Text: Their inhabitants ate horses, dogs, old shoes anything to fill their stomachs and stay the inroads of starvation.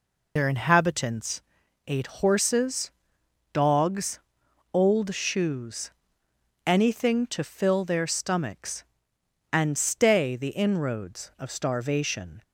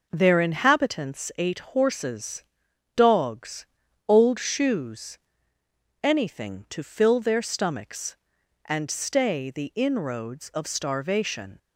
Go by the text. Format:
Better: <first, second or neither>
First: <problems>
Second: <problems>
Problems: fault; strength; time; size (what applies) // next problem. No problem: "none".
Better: second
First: loses the start of "Their"; at 0.3 s; 85 ms // pauses between "inhabitants" and "ate"; at 1.4 s; 0.44 s long // pauses between "shoes" and "anything"; noticeable; at 5.8 s; 0.76 s long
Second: pauses between "shoes" and "anything"; noticeable; at 5.1 s; 0.84 s long